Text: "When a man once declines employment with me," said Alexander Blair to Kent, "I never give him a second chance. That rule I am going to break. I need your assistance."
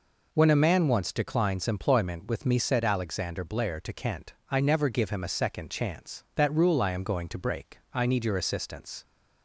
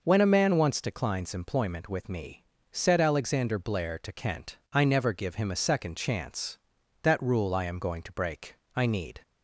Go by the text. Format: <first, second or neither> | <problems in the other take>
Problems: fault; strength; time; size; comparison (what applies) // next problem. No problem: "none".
first | stops before "your assistance"; at 9.2 s